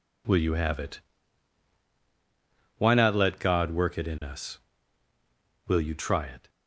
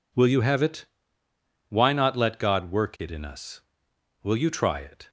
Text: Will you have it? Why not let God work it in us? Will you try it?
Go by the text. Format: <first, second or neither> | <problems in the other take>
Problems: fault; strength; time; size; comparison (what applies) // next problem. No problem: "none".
neither | none